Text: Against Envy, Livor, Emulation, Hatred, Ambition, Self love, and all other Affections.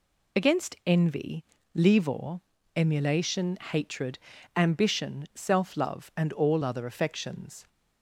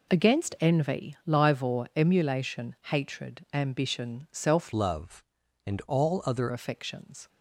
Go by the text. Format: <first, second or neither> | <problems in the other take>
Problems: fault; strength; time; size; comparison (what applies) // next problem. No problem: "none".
first | changes voice from "love" to "other"; from 4.7 to 6.4 s; 1.7 s long